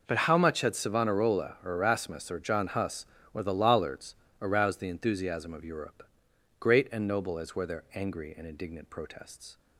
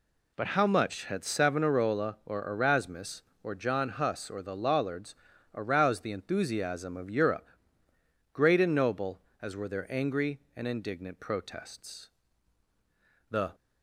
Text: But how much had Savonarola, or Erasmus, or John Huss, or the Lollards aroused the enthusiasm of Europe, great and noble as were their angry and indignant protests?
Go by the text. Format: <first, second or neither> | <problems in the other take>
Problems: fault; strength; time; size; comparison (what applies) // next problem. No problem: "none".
first | pauses between "Lollards" and "aroused"; at 5.1 s; 0.40 s long; slight in the first // goes on to say "The"; slight; from 13.2 s on; 0.24 s long